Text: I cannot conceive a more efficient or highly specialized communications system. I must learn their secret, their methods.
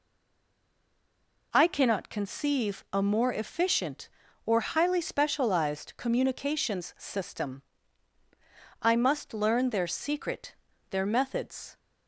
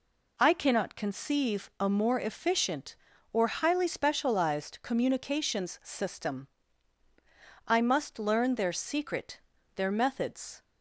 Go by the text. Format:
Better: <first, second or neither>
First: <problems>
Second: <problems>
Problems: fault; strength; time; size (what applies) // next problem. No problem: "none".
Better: second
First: stays silent before the first word; noticeable; until 1.5 s; 1.5 s long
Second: none